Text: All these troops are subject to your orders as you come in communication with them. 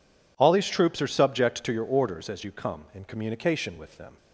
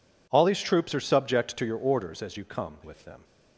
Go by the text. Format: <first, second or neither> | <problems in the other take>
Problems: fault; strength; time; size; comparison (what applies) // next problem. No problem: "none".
first | skips "in communication"; at 2.8 s